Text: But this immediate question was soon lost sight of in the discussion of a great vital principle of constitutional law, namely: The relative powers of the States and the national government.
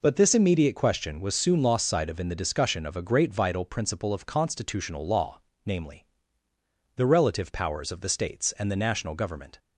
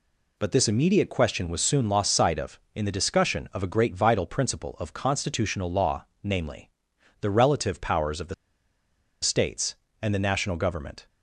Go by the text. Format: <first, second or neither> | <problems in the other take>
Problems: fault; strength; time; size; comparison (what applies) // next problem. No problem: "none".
first | pauses between "the" and "States"; noticeable; at 8.3 s; 0.89 s long